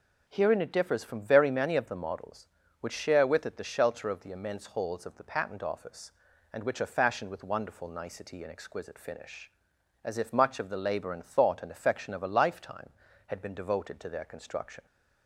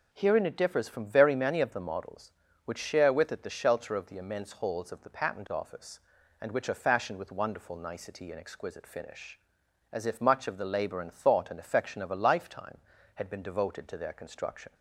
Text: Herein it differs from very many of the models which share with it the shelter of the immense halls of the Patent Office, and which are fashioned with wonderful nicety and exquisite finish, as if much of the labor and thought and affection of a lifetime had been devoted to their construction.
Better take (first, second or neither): neither